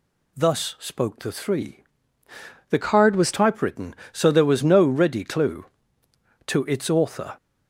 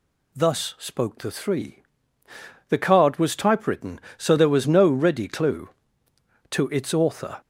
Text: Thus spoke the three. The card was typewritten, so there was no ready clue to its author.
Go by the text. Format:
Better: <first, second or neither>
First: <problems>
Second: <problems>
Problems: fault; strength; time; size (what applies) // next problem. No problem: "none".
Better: second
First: changes voice from "card" to "was"; from 2.8 to 3.3 s; 0.5 s long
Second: none